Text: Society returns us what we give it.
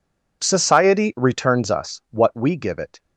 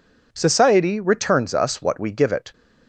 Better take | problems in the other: neither | none

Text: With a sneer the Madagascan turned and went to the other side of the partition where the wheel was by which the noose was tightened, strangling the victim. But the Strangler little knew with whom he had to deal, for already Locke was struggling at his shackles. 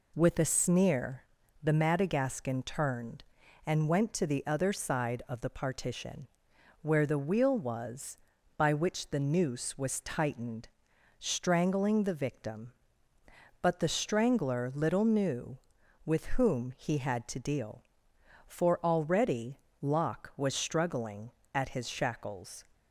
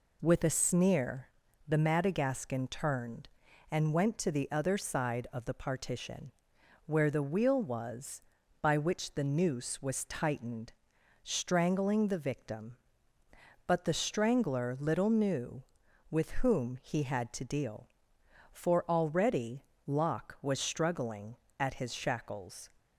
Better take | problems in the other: neither | pauses between "sneer" and "the"; the same in both // pauses between "partition" and "where"; noticeable; the same in both // pauses between "already" and "Locke"; slight; the same in both

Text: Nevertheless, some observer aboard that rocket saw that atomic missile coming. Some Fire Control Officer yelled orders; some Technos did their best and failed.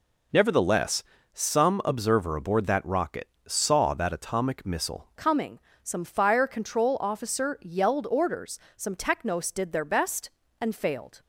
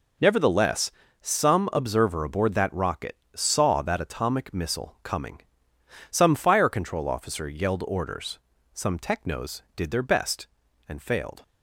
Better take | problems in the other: second | pauses between "rocket" and "saw"; slight; at 3.2 s; 0.16 s long; slight in the second // changes voice at "coming"; from 5.1 s on; 6.1 s long

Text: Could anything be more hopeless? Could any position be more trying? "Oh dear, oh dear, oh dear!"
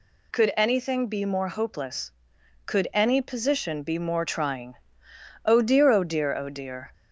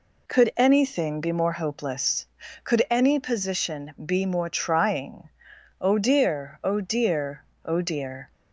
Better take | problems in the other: neither | none

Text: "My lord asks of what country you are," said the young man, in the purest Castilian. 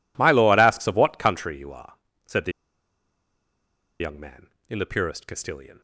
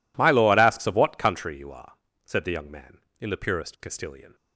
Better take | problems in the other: second | pauses between "the" and "young"; strong; at 2.5 s; 1.4 s long

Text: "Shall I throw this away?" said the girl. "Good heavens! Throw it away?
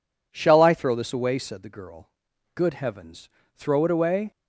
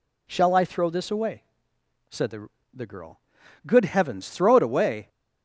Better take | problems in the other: first | says "the" twice; at 2.7 s

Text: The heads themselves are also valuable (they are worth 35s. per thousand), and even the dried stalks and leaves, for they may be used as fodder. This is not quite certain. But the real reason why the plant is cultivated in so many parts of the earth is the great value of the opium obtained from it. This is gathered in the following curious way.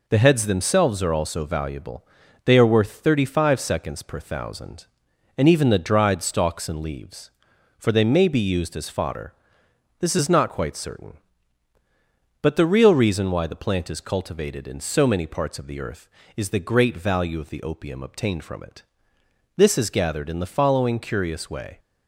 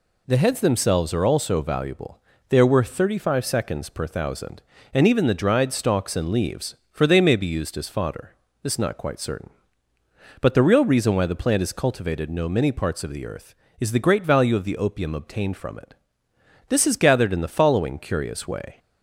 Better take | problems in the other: first | says "no" for "so"; at 12.3 s

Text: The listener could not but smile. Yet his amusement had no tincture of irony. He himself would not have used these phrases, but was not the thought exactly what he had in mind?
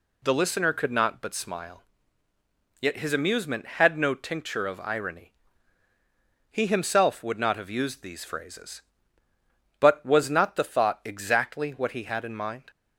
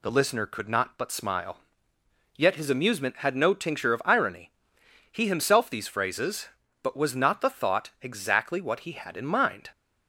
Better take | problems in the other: first | skips "would not have used"; at 5.6 s

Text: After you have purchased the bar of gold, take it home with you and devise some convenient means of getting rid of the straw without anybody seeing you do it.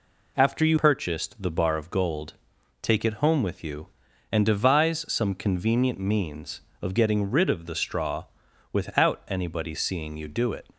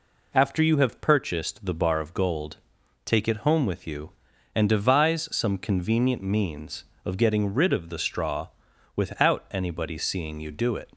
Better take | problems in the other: second | skips "have"; at 0.7 s // pauses between "straw" and "without"; noticeable; at 8.2 s; 0.48 s long; noticeable in the second

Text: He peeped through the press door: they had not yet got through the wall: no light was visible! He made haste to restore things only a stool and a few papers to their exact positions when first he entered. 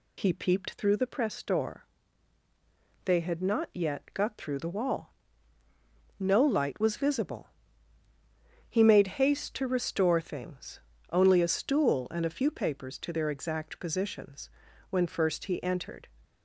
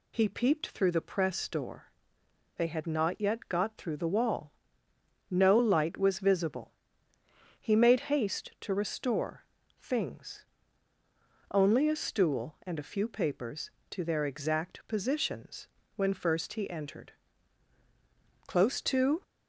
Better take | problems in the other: first | pauses between "restore" and "things"; slight; at 9.4 s; 0.34 s long // pauses between "things" and "only"; at 10.4 s; 1.0 s long; slight in the first // pauses between "positions" and "when"; slight; at 15.6 s; 0.30 s long; also in the first // goes on to say "Close to"; noticeable; from 18.4 s on; 0.76 s long

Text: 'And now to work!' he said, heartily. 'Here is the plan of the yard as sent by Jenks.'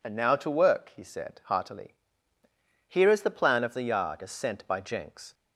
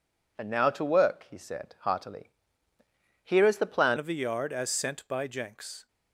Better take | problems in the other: first | changes voice at "of"; from 3.9 s on; 1.9 s long

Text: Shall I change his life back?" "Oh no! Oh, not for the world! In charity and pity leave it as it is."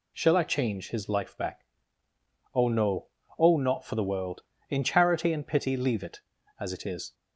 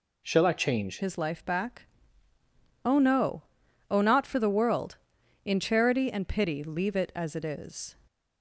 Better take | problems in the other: first | changes voice at "his"; from 1.0 s on; 6.9 s long

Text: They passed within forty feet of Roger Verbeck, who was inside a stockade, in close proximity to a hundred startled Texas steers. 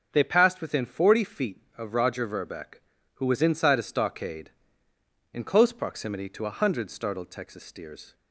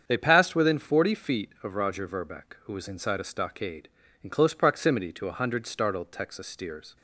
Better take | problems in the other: neither | starts louder than the rest; the same in both

